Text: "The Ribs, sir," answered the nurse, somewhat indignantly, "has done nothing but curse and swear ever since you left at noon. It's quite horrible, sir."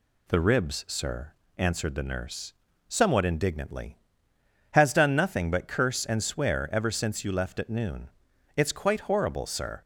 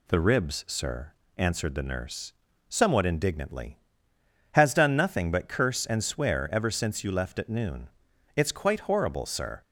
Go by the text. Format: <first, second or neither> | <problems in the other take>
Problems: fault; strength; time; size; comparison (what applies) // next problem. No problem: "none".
neither | none